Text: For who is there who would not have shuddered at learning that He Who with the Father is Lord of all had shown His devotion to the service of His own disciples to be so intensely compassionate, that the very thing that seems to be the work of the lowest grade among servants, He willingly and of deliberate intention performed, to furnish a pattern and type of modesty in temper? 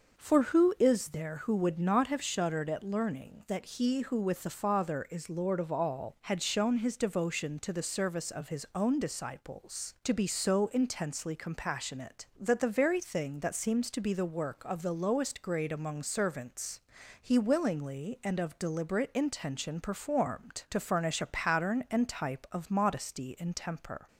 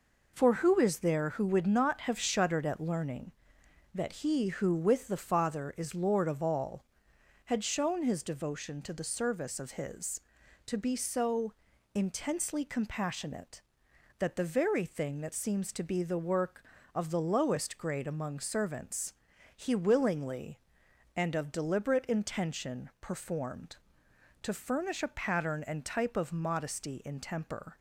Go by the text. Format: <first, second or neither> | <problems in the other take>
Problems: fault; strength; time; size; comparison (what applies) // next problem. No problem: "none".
first | skips "own disciples"; at 10.4 s // pauses between "so" and "intensely"; at 11.5 s; 0.42 s long